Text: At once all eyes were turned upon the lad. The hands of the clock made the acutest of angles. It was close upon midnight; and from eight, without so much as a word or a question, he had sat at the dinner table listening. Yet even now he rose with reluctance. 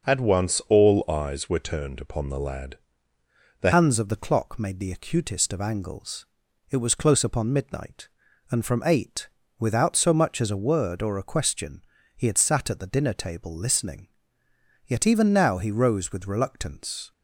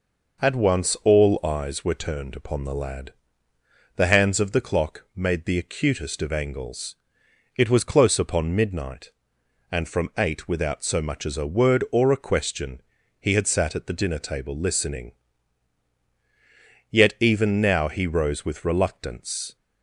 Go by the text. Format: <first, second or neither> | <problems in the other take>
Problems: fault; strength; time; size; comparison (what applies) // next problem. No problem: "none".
second | changes voice at "hands"; from 3.7 s on; 13.4 s long